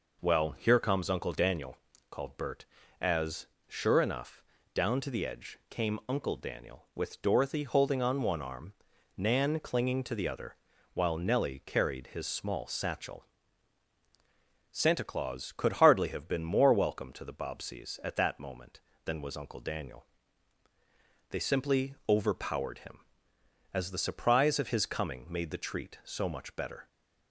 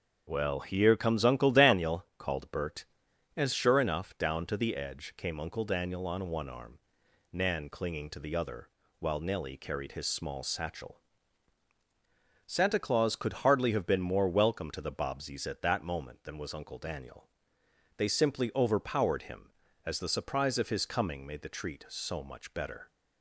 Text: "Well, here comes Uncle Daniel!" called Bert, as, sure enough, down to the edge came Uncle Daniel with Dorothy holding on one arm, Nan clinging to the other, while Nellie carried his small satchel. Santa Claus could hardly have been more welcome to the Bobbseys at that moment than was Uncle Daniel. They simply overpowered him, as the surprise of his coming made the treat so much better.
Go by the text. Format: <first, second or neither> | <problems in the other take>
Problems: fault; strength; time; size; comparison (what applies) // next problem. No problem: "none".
first | starts louder than the rest; strong; until 1.2 s; 7 dB // skips "with Dorothy holding"; at 6.0 s